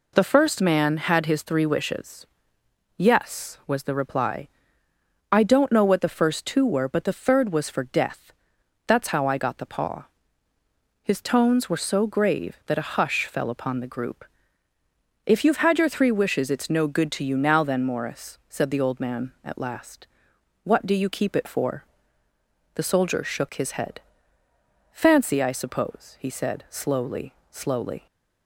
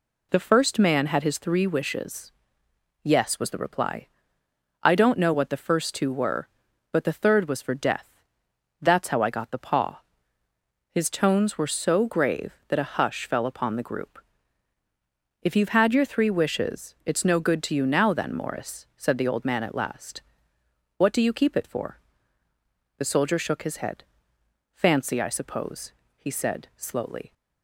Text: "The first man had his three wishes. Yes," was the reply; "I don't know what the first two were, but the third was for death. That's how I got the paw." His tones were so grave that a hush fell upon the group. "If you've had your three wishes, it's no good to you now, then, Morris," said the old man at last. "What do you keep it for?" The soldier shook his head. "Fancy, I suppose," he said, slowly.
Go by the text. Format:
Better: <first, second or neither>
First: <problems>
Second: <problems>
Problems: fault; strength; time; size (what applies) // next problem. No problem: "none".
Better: second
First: says "slowly" twice; at 27.4 s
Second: none